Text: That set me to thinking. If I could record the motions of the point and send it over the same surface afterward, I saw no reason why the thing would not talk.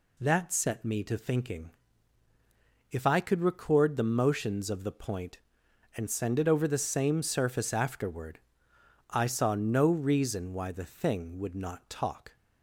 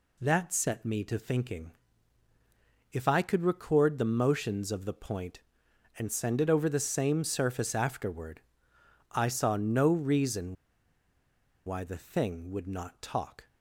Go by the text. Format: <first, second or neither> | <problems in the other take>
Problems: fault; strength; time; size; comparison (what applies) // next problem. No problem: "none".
first | pauses between "reason" and "why"; at 10.5 s; 1.1 s long